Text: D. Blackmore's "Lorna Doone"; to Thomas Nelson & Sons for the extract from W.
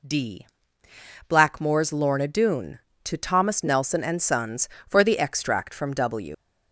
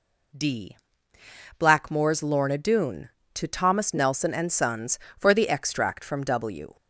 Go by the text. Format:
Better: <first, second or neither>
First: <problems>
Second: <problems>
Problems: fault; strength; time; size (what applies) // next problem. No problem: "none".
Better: second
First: leaves "W" unfinished; at 6.3 s; 110 ms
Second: none